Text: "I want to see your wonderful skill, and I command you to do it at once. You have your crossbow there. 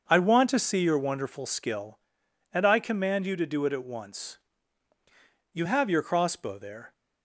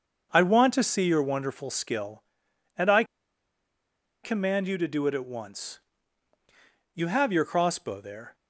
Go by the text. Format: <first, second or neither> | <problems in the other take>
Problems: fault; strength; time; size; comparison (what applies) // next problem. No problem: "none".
first | starts louder than the rest; until 1.3 s; 6.5 dB; also in the first // pauses between "I" and "command"; at 3.0 s; 1.2 s long